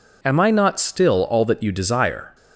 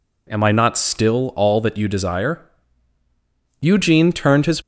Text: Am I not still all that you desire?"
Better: first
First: none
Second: goes on to say "Eugene turned his"; noticeable; from 3.6 s on; 1.0 s long

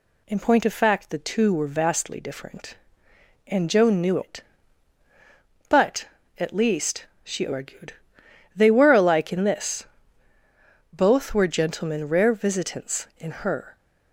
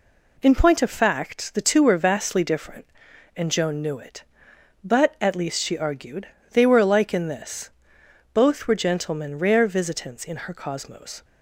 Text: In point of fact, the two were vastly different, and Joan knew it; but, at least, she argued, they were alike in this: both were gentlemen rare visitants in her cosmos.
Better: second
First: stops before "cosmos"; at 13.7 s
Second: none

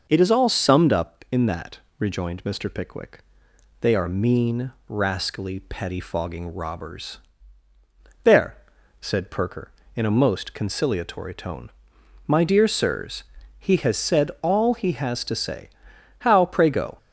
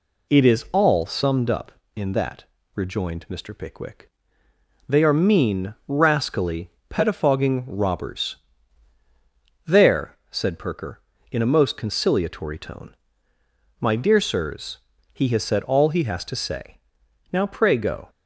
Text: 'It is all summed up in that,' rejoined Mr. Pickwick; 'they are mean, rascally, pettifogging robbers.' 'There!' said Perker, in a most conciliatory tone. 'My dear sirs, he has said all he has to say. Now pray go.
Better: second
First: starts louder than the rest; noticeable; until 1.1 s; 6 dB // says "How" for "Now"; at 16.1 s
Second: none

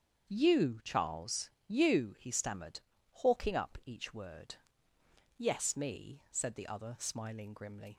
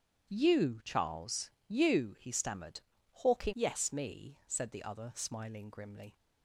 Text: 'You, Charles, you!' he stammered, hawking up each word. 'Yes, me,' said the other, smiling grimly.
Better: first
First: starts louder than the rest; strong; until 1.3 s; 7 dB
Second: starts louder than the rest; strong; until 1.3 s; 9.5 dB // skips "up each word"; at 3.5 s

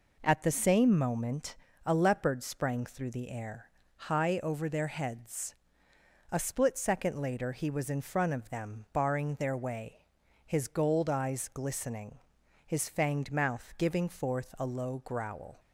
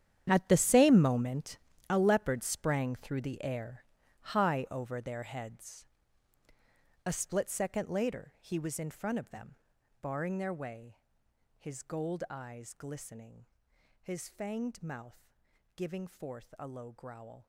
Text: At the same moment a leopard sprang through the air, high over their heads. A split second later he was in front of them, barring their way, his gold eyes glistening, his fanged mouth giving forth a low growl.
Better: first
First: pauses between "moment" and "a"; slight; at 1.5 s; 0.30 s long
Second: gets quieter; strong; throughout; 15.5 dB // pauses between "moment" and "a"; slight; at 1.5 s; 0.32 s long // pauses between "mouth" and "giving"; at 15.3 s; 0.44 s long

